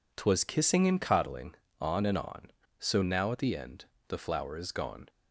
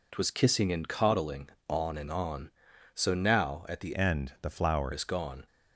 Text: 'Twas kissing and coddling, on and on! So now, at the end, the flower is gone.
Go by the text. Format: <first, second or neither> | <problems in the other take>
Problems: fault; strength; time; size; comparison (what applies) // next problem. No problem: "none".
first | changes voice from "end" to "flower"; from 3.9 to 4.9 s; 1.0 s long